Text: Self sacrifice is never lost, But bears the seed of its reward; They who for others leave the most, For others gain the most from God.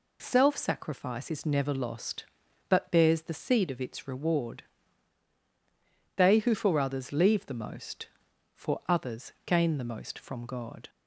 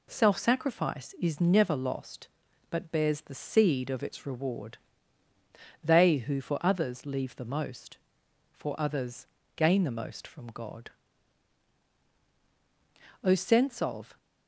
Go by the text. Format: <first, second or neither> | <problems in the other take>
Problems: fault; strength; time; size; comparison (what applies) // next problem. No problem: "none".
first | pauses between "others" and "gain"; slight; at 9.2 s; 0.28 s long // goes on to say "O sense of"; noticeable; from 13.2 s on; 0.94 s long